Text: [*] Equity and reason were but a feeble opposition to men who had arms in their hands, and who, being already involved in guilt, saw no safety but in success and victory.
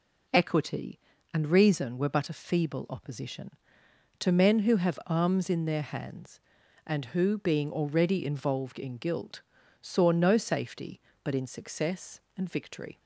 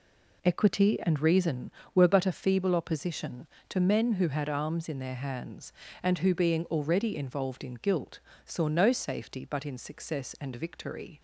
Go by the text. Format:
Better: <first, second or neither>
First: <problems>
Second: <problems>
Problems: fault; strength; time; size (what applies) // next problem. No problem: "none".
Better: second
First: says "have" for "had"; at 4.7 s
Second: none